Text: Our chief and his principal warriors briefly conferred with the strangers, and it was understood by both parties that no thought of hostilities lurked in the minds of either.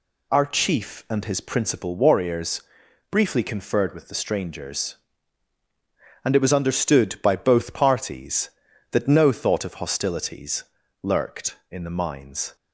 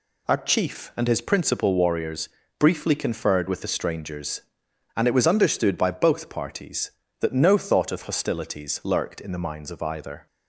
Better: second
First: pauses between "warriors" and "briefly"; noticeable; at 2.6 s; 0.48 s long // pauses between "hostilities" and "lurked"; slight; at 10.6 s; 0.36 s long // stops before "of either"; at 12.5 s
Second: pauses between "warriors" and "briefly"; slight; at 2.2 s; 0.30 s long

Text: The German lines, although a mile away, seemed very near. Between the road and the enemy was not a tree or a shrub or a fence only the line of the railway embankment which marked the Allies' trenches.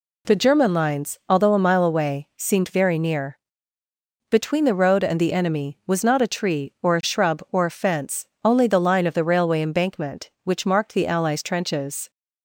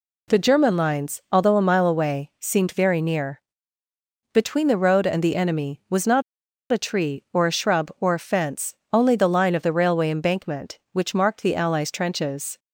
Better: first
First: pauses between "fence" and "only"; slight; at 8.2 s; 0.18 s long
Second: pauses between "not" and "a"; noticeable; at 6.2 s; 0.48 s long // pauses between "fence" and "only"; slight; at 8.7 s; 0.18 s long

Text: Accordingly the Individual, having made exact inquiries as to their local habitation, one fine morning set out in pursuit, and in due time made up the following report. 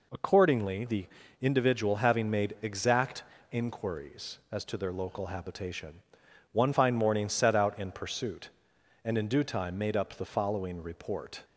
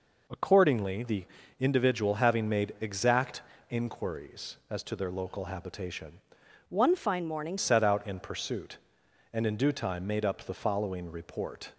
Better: first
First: pauses between "the" and "Individual"; slight; at 1.0 s; 0.34 s long // pauses between "exact" and "inquiries"; slight; at 3.2 s; 0.30 s long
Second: pauses between "the" and "Individual"; slight; at 1.2 s; 0.34 s long // pauses between "exact" and "inquiries"; slight; at 3.4 s; 0.30 s long // changes voice from "one" to "morning"; from 6.6 to 7.5 s; 0.9 s long

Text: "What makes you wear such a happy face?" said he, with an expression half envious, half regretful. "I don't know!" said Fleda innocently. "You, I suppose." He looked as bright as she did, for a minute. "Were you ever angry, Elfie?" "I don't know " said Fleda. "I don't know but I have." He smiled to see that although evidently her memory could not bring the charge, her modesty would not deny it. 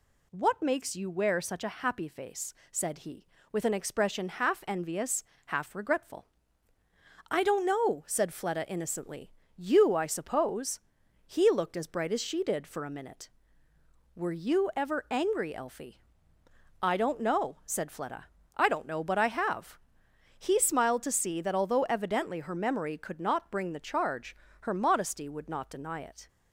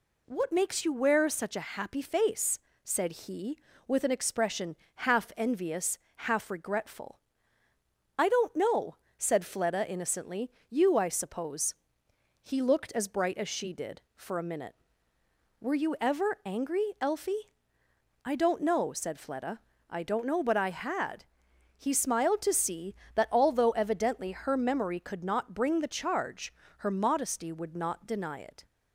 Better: first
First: none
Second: pauses between "expression" and "half"; slight; at 4.7 s; 0.20 s long // says "had" for "have"; at 20.6 s

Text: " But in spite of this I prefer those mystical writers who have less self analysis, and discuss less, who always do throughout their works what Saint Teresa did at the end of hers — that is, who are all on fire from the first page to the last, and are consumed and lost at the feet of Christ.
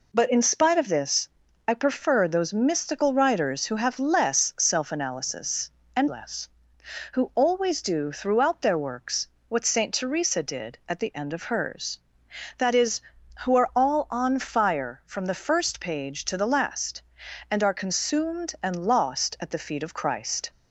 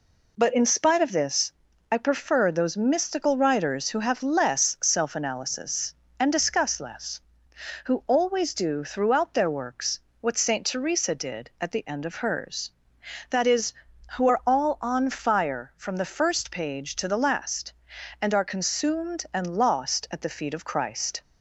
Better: second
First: pauses between "this" and "I"; at 1.2 s; 0.40 s long // skips "discuss"; at 6.0 s // pauses between "works" and "what"; slight; at 9.2 s; 0.22 s long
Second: pauses between "this" and "I"; at 1.5 s; 0.40 s long // pauses between "works" and "what"; slight; at 9.9 s; 0.22 s long

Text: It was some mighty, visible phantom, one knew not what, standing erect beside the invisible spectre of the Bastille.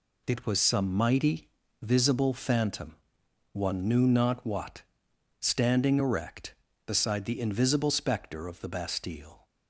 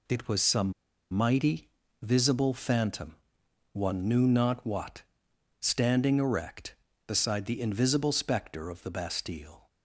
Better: first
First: none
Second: pauses between "some" and "mighty"; at 0.7 s; 0.40 s long

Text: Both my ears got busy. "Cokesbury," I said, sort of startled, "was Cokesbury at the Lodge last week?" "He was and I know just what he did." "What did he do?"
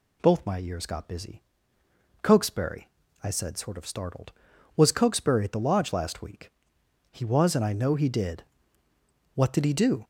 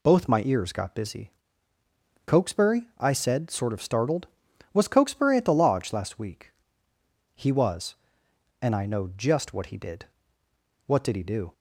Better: second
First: skips "just what"; at 7.9 s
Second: none

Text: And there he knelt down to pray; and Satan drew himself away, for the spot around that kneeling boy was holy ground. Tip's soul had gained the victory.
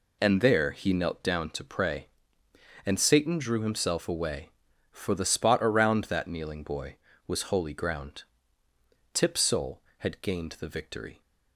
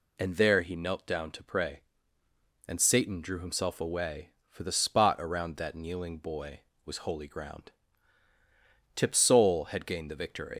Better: first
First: none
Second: leaves "victory" unfinished; at 10.5 s; 95 ms

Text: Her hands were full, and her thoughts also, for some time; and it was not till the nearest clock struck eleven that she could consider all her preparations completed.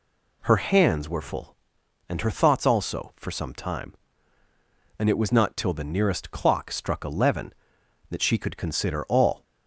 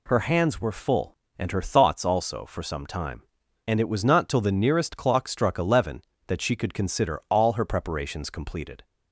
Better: second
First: stops before "her preparations completed"; at 9.4 s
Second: none

